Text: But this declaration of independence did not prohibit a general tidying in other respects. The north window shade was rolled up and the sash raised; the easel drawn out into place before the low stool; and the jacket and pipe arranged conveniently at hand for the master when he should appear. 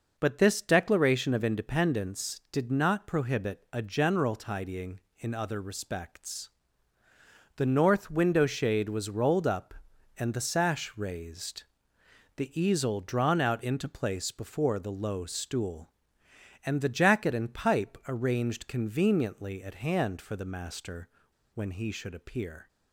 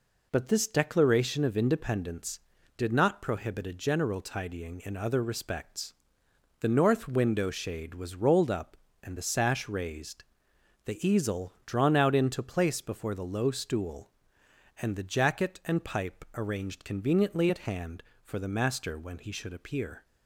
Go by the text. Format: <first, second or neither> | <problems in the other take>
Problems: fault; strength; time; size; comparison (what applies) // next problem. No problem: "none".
second | pauses between "master" and "when"; at 21.0 s; 0.45 s long